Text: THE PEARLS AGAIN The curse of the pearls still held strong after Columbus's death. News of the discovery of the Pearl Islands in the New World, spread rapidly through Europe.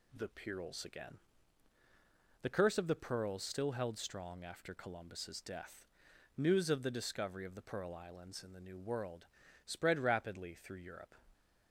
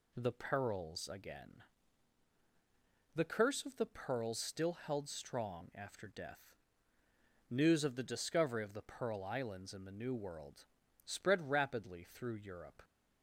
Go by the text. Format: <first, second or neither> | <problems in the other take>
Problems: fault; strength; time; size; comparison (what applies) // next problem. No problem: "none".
first | pauses between "AGAIN" and "The"; strong; at 1.6 s; 1.5 s long; also in the first // skips "Columbus's"; at 6.0 s